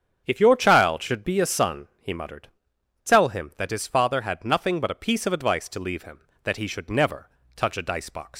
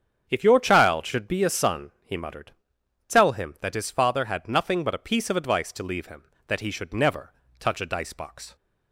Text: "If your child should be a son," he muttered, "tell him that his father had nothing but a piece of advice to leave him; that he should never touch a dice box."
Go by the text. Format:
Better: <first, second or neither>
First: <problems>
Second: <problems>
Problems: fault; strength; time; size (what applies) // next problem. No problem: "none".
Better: second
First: starts louder than the rest; strong; until 1.2 s; 8 dB // pauses between "never" and "touch"; slight; at 7.2 s; 0.28 s long // leaves "box" unfinished; at 8.3 s; 115 ms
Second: starts louder than the rest; strong; until 1.3 s; 8 dB // pauses between "never" and "touch"; slight; at 7.3 s; 0.28 s long